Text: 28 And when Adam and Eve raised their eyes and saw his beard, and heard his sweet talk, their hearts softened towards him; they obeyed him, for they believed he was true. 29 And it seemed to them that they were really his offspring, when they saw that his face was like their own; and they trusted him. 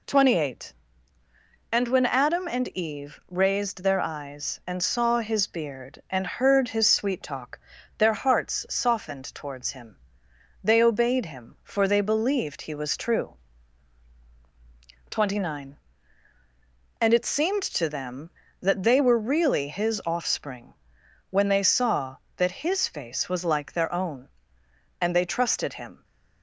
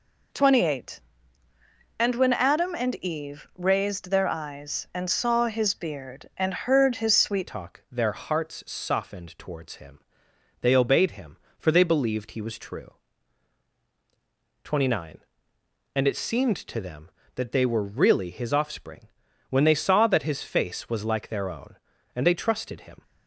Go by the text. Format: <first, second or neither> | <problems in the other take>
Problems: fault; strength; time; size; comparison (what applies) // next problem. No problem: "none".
first | changes voice at "talk"; from 7.4 s on; 15.6 s long